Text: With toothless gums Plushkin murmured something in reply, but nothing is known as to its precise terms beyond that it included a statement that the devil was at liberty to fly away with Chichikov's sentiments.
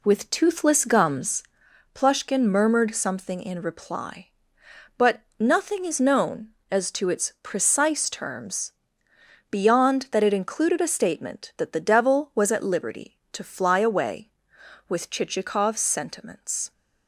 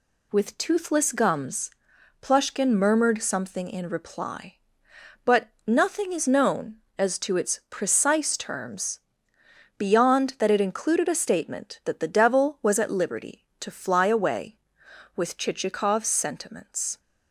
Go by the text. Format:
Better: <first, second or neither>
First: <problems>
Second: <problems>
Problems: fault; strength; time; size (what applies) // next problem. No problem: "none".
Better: second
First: starts louder than the rest; slight; until 1.7 s; 2.5 dB // pauses between "gums" and "Plushkin"; noticeable; at 1.4 s; 0.50 s long // pauses between "but" and "nothing"; slight; at 5.1 s; 0.18 s long // pauses between "terms" and "beyond"; noticeable; at 8.7 s; 0.78 s long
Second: pauses between "gums" and "Plushkin"; noticeable; at 1.7 s; 0.50 s long // pauses between "but" and "nothing"; slight; at 5.4 s; 0.18 s long // pauses between "terms" and "beyond"; noticeable; at 8.9 s; 0.78 s long